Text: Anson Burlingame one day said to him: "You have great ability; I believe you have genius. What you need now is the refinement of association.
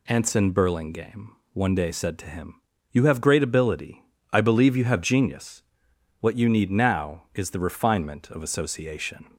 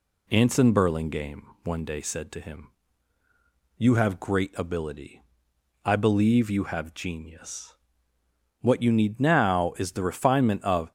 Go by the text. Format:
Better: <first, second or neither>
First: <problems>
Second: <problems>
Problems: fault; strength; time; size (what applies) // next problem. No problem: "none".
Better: first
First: pauses between "Burlingame" and "one"; slight; at 1.3 s; 0.22 s long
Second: pauses between "Burlingame" and "one"; slight; at 1.4 s; 0.20 s long // stops before "association"; at 10.8 s